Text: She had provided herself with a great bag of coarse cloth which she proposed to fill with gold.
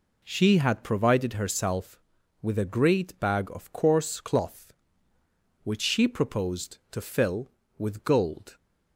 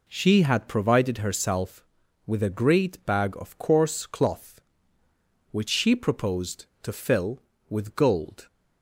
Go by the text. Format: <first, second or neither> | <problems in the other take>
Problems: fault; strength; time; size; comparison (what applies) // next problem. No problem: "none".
neither | none